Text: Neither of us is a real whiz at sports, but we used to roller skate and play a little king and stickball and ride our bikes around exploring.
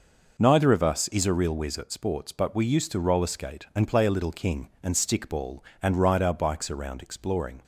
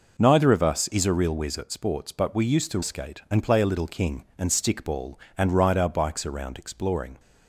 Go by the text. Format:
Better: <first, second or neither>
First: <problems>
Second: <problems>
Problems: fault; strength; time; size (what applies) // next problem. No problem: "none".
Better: first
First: none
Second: skips "roller"; at 2.8 s